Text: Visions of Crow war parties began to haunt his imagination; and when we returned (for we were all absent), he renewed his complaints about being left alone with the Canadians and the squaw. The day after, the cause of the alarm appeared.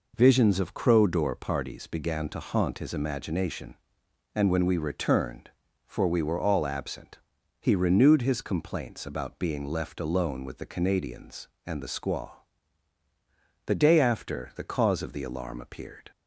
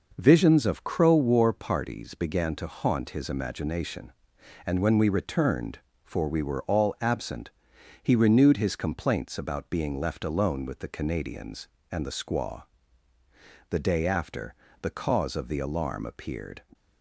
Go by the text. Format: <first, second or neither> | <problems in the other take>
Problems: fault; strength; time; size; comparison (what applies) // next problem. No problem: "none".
second | says "door" for "war"; at 1.0 s